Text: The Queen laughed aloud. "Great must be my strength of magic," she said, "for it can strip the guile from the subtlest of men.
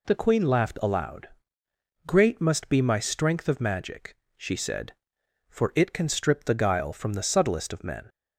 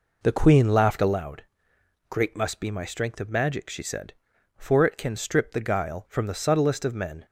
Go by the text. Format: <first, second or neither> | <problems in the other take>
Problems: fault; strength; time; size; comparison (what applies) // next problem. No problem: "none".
first | starts louder than the rest; noticeable; until 1.2 s; 4.5 dB